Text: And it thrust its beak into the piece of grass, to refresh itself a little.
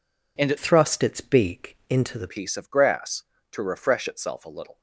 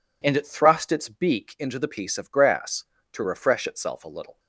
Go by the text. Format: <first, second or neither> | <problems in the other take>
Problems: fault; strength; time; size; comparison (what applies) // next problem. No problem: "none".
second | changes voice from "thrust" to "the"; from 0.5 to 2.2 s; 1.7 s long